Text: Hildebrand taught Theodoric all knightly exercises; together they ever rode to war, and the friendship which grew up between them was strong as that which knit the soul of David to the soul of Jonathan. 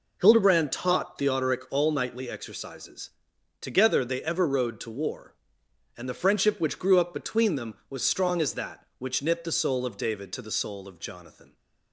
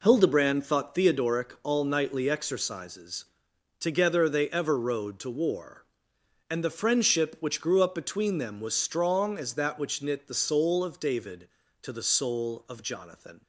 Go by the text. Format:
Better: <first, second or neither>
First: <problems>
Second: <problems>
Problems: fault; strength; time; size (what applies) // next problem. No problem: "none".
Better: first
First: none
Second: says "thought" for "taught"; at 0.6 s